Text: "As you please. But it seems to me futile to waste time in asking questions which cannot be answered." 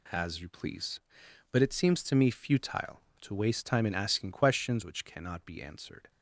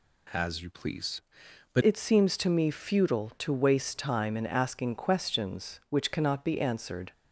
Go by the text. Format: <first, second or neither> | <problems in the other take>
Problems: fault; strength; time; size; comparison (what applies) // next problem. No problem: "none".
first | changes voice at "it"; from 1.8 s on; 5.3 s long